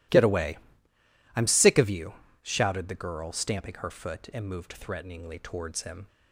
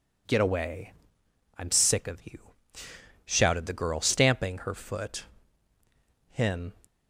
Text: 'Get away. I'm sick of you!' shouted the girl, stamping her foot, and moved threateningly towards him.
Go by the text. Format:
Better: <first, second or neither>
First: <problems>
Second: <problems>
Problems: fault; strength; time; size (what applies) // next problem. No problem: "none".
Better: first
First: none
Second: skips "and moved threateningly towards"; at 5.7 s